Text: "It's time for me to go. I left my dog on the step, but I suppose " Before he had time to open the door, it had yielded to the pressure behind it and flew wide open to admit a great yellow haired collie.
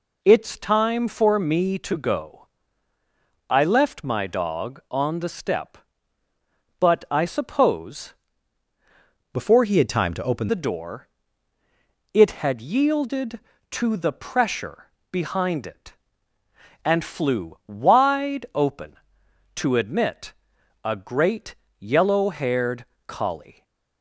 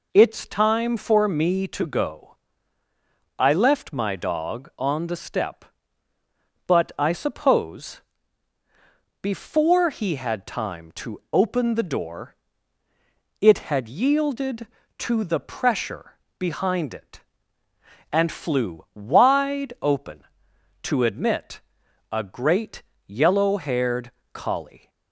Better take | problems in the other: second | changes voice from "Before" to "open"; from 9.3 to 10.4 s; 1.1 s long // pauses between "pressure" and "behind"; slight; at 14.8 s; 0.22 s long; slight in the second // pauses between "admit" and "a"; noticeable; at 20.3 s; 0.50 s long; noticeable in the second // pauses between "great" and "yellow"; slight; at 21.5 s; 0.24 s long; slight in the second // pauses between "haired" and "collie"; slight; at 22.8 s; 0.20 s long; slight in the second

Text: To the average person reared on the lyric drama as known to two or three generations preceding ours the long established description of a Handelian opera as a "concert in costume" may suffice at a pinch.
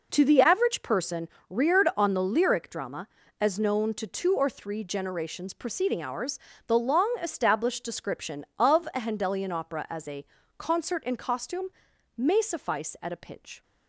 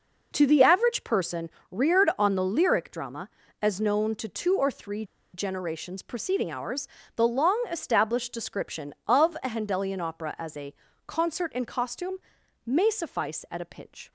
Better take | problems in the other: first | pauses between "person" and "reared"; slight; at 1.4 s; 0.20 s long; slight in the first // pauses between "three" and "generations"; slight; at 5.0 s; 0.30 s long // pauses between "ours" and "the"; slight; at 6.8 s; 0.28 s long; slight in the first // pauses between "a" and "concert"; slight; at 10.7 s; 0.32 s long; slight in the first // pauses between "costume" and "may"; noticeable; at 12.1 s; 0.50 s long; noticeable in the first

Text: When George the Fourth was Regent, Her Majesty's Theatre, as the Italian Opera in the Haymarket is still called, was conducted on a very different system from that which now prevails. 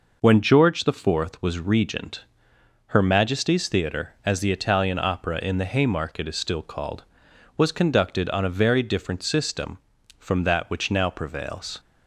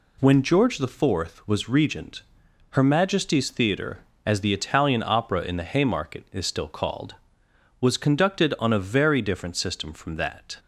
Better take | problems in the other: first | stops before "which now prevails"; at 10.5 s

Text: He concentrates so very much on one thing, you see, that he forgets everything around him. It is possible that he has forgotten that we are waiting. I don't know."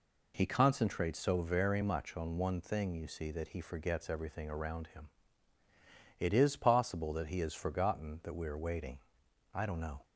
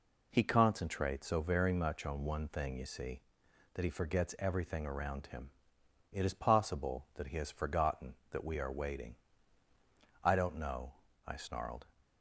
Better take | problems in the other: first | goes on to say "I snarled"; from 11.2 s on; 0.58 s long

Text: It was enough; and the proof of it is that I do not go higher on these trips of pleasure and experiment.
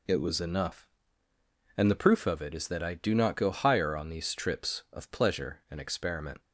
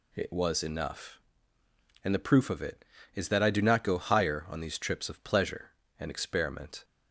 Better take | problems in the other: neither | none

